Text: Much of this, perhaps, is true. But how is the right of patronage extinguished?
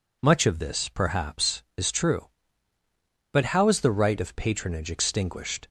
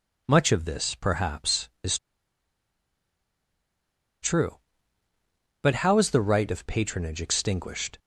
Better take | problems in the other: first | pauses between "is" and "true"; strong; at 1.9 s; 2.2 s long

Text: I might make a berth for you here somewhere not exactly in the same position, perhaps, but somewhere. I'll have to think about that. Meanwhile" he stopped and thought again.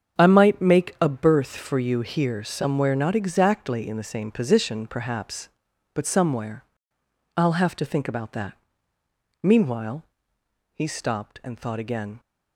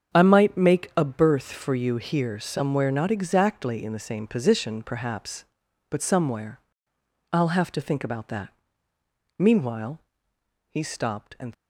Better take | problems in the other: first | starts louder than the rest; strong; until 1.2 s; 7.5 dB; strong in the first // pauses between "Meanwhile" and "he"; noticeable; at 9.9 s; 0.70 s long; noticeable in the first // stops before "thought again"; at 11.5 s

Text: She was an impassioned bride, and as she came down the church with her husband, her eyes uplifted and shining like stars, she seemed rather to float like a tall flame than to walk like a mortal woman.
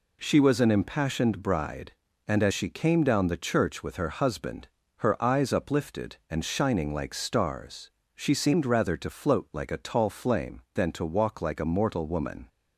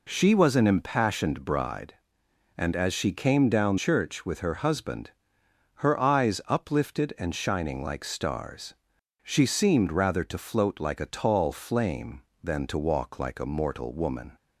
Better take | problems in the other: first | skips "the"; at 3.7 s

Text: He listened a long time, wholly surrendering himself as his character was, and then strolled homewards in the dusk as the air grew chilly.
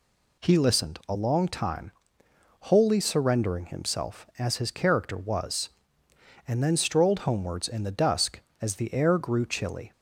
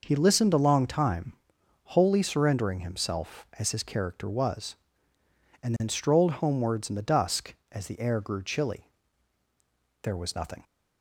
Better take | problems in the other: first | goes on to say "There was nothing"; from 10.0 s on; 0.60 s long

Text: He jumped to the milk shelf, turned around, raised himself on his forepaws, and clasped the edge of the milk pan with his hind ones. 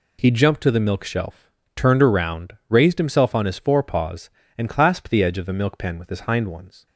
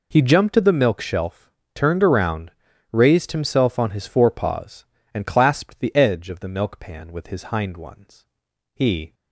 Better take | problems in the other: first | goes on to say "He"; slight; from 8.7 s on; 0.38 s long

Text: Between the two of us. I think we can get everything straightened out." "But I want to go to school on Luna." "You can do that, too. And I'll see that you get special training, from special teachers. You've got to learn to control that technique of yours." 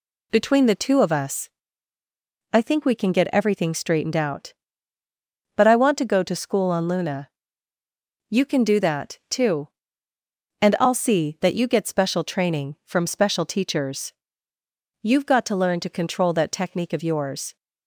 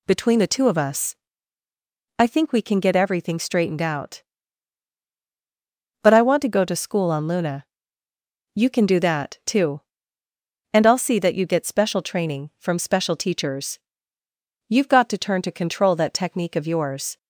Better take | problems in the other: first | says "turn" for "learn"; at 15.1 s

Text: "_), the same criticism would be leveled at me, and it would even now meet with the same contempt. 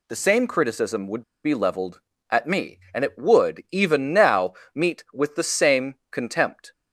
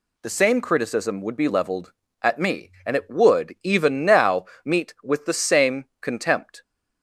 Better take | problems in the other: second | pauses between "would" and "be"; slight; at 1.2 s; 0.22 s long // pauses between "now" and "meet"; slight; at 4.5 s; 0.20 s long; slight in the second // pauses between "same" and "contempt"; slight; at 5.9 s; 0.16 s long; slight in the second

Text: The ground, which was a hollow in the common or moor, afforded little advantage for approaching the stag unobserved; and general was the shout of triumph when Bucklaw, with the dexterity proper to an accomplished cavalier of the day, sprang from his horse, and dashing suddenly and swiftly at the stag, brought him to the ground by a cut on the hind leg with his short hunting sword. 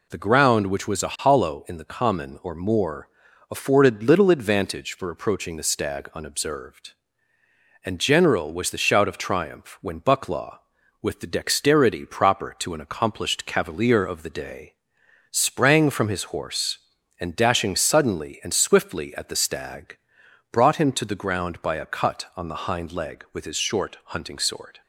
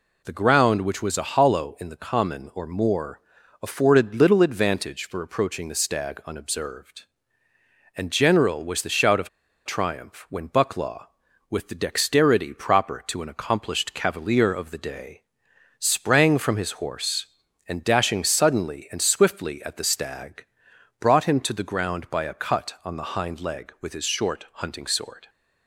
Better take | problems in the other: first | pauses between "of" and "triumph"; at 9.2 s; 0.37 s long

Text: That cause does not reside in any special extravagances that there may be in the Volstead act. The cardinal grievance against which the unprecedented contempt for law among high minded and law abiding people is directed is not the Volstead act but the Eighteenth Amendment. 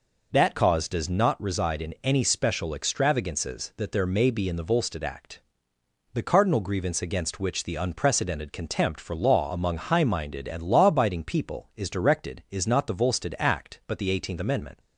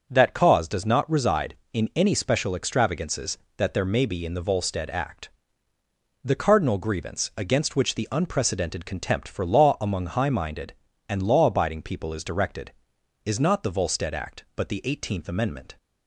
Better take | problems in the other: neither | none

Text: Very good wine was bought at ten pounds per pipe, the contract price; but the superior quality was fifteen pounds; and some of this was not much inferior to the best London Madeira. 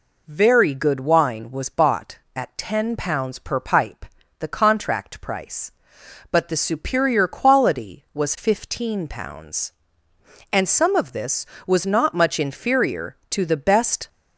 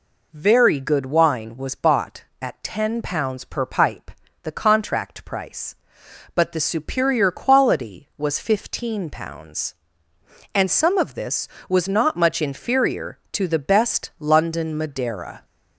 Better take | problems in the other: second | stops before "London Madeira"; at 14.0 s

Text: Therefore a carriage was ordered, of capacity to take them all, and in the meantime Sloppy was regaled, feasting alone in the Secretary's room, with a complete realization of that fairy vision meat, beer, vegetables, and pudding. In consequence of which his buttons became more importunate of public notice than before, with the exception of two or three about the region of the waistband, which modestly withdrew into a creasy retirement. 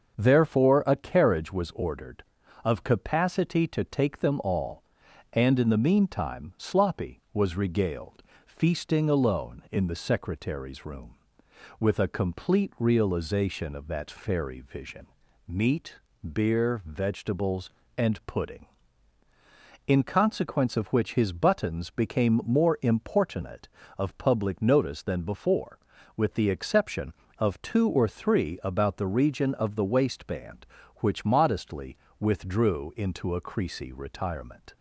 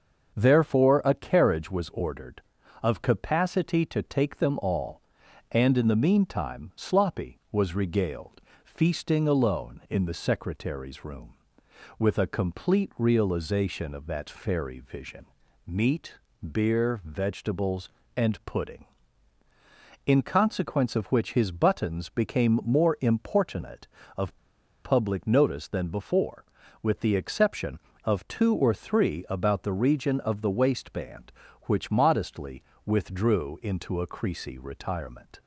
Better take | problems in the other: first | starts louder than the rest; until 1.3 s; 6.5 dB; also in the first // pauses between "vision" and "meat"; at 15.2 s; 0.42 s long; also in the first // pauses between "of" and "public"; noticeable; at 24.3 s; 0.49 s long // pauses between "modestly" and "withdrew"; slight; at 32.6 s; 0.22 s long; slight in the first

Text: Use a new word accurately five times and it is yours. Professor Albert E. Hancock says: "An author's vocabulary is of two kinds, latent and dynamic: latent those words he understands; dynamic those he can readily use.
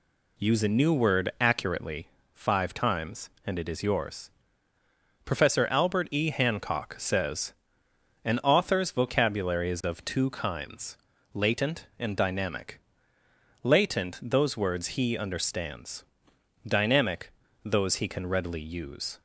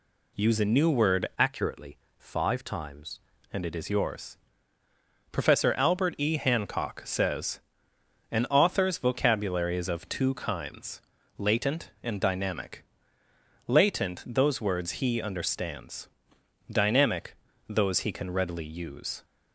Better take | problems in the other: first | changes voice from "accurately" to "times"; from 1.3 to 3.1 s; 1.8 s long // pauses between "accurately" and "five"; slight; at 1.9 s; 0.22 s long; slight in the first // pauses between "dynamic" and "those"; slight; at 17.3 s; 0.32 s long; slight in the first

